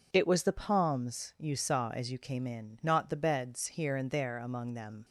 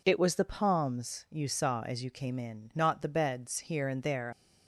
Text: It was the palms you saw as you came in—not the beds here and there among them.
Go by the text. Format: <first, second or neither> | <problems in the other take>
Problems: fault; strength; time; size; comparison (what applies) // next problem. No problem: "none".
first | stops before "among them"; at 4.3 s